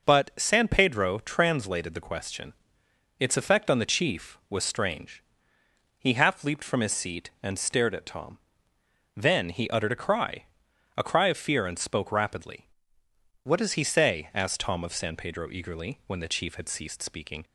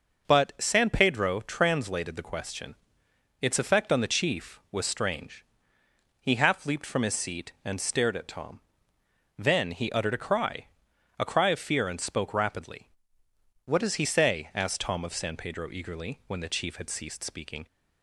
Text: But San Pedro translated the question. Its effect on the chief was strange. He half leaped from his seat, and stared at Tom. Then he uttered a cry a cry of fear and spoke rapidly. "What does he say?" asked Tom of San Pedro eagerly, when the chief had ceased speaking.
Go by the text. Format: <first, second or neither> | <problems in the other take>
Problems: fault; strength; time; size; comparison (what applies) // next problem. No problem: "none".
neither | pauses between "cry" and "a"; noticeable; the same in both